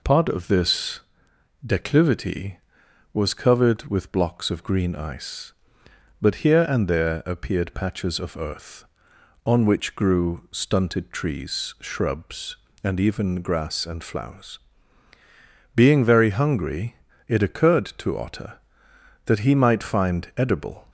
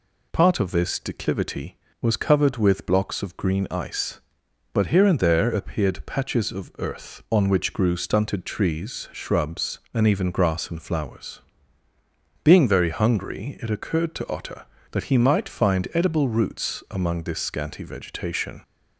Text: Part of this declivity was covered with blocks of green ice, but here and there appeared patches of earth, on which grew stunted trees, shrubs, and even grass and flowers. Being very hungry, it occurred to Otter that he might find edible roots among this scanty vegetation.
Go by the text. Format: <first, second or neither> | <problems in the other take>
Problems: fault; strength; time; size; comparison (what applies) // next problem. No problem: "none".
second | pauses between "this" and "declivity"; noticeable; at 0.9 s; 0.66 s long // stops before "roots among this scanty vegetation"; at 20.8 s